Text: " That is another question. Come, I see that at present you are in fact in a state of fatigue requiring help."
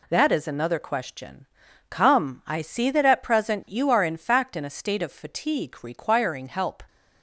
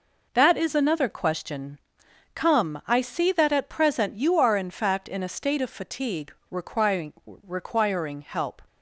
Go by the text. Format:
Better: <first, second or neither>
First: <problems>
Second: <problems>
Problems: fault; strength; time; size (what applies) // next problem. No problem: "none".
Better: first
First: none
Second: pauses between "fatigue" and "requiring"; slight; at 6.3 s; 0.18 s long // says "requiring" twice; at 7.2 s